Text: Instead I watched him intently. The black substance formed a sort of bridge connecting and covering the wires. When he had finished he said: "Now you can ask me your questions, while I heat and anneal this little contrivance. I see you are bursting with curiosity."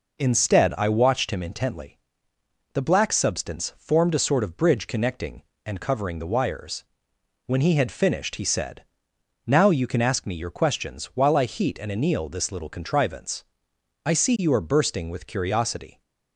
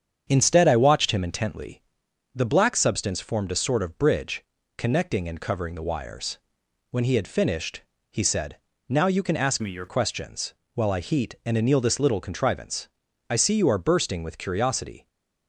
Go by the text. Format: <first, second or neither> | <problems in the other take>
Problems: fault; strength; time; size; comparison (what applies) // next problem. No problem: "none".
first | starts louder than the rest; strong; until 1.2 s; 8 dB // pauses between "bridge" and "connecting"; slight; at 4.4 s; 0.32 s long // pauses between "finished" and "he"; slight; at 7.8 s; 0.30 s long // changes voice from "me" to "your"; from 9.6 to 9.8 s; 0.2 s long